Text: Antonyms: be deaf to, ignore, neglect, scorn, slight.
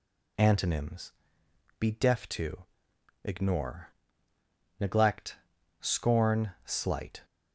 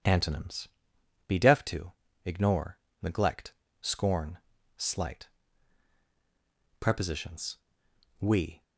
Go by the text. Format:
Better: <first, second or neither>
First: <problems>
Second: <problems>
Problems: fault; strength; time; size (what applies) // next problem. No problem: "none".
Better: first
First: none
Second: goes on to say "Prepositions We"; strong; from 6.7 s on; 1.8 s long